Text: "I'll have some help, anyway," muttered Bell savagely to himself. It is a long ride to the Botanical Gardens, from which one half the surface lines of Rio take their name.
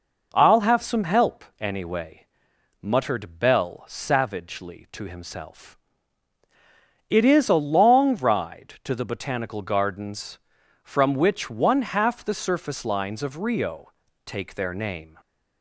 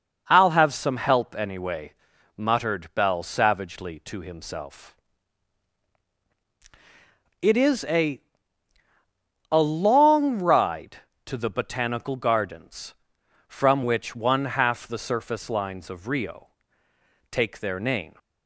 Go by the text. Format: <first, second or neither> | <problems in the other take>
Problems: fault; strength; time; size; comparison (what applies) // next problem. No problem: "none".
first | says "a" twice; at 9.5 s // pauses between "Rio" and "take"; noticeable; at 16.5 s; 0.80 s long; slight in the first